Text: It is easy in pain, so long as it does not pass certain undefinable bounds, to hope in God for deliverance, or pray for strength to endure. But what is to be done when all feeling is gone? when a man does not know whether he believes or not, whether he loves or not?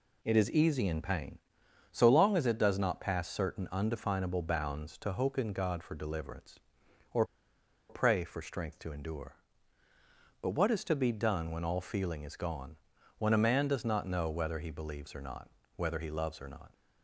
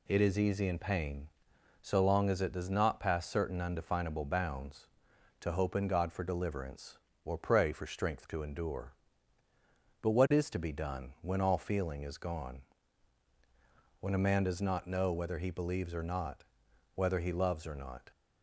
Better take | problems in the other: second | pauses between "or" and "pray"; noticeable; at 7.2 s; 0.65 s long

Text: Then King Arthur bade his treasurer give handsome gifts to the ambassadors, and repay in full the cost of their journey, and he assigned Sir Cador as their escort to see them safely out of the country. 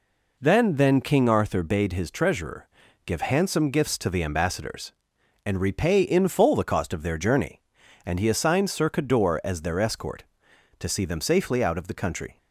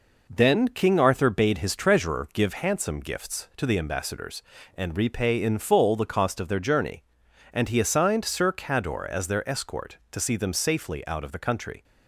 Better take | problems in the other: second | says "Then" twice; at 0.7 s // pauses between "treasurer" and "give"; at 2.6 s; 0.38 s long

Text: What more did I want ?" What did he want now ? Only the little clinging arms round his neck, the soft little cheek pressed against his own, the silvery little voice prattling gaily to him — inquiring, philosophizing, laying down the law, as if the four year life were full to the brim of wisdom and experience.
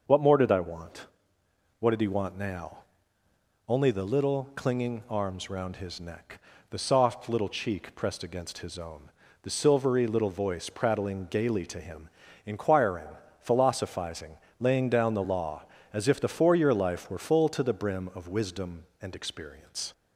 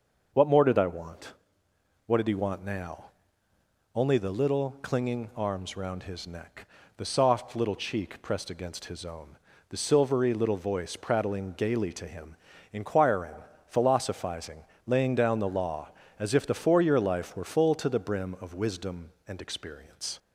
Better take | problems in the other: neither | none

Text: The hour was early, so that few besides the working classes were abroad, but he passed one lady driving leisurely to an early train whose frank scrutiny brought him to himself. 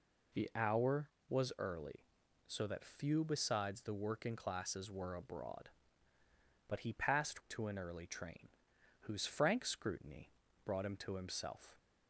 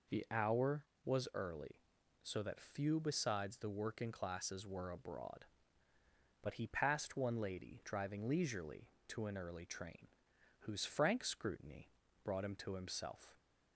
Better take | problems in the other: second | skips "one lady driving leisurely"; at 7.4 s // pauses between "train" and "whose"; noticeable; at 8.4 s; 0.54 s long; noticeable in the second // pauses between "scrutiny" and "brought"; slight; at 10.2 s; 0.36 s long; slight in the second

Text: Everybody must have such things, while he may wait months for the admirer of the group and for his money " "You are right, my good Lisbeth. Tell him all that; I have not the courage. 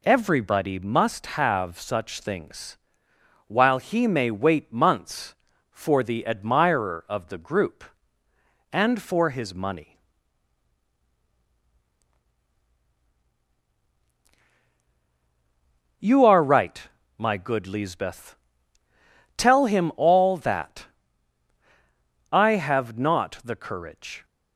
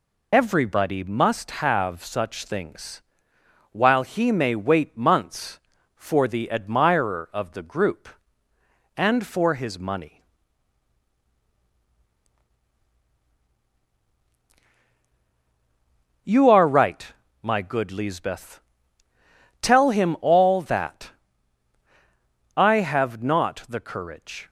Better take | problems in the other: first | loses the start of "Everybody"; at 0.3 s; 40 ms

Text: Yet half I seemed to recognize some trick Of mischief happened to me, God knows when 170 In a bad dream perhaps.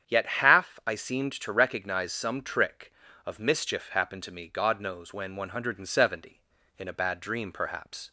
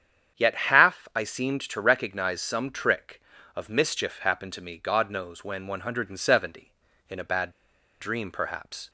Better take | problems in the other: first | starts louder than the rest; strong; until 1.4 s; 8 dB; strong in the first // pauses between "bad" and "dream"; noticeable; at 7.5 s; 0.48 s long

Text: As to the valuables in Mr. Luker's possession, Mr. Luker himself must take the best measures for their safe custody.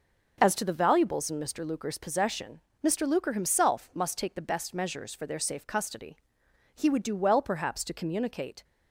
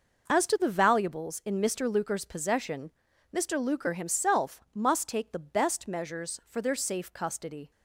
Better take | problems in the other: second | goes on to say "He would do well perhaps to communicate"; strong; from 6.7 s on; 1.8 s long

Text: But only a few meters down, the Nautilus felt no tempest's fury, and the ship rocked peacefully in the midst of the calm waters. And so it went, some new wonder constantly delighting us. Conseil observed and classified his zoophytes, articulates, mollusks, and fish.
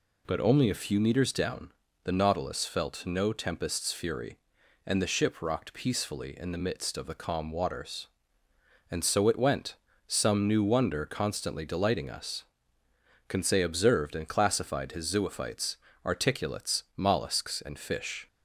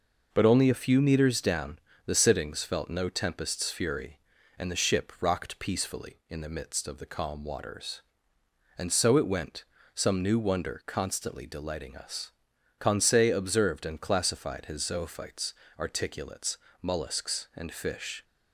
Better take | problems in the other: first | says "Sittings" for "Nautilus"; at 2.1 s

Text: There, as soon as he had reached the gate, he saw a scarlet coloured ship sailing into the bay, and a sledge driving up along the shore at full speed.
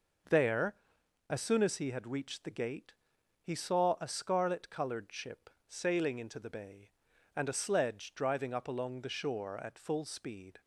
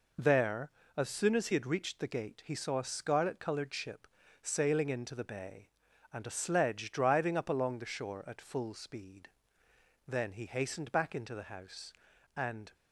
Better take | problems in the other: first | pauses between "ship" and "sailing"; slight; at 4.0 s; 0.36 s long; slight in the first // goes on to say "Then he hastened back into the house and"; strong; from 10.0 s on; 2.6 s long

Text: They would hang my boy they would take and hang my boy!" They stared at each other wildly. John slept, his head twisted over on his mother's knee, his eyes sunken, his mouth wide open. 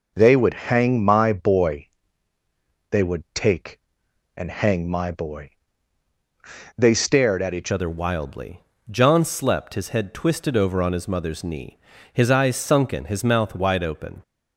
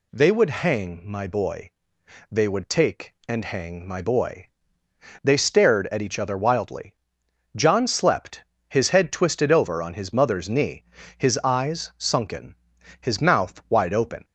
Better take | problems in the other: second | pauses between "boy" and "they"; at 1.8 s; 1.0 s long; noticeable in the second // changes voice at "other"; from 7.7 s on; 6.5 s long

